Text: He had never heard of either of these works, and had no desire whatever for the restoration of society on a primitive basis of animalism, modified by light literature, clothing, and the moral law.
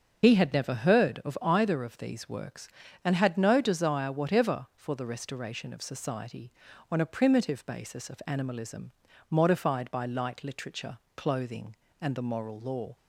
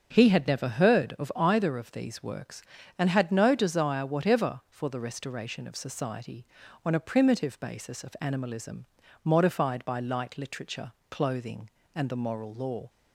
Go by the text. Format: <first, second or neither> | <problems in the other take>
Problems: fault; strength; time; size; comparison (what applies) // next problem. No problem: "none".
second | loses the start of "He"; at 0.2 s; 70 ms // starts louder than the rest; until 1.2 s; 6.5 dB; also in the second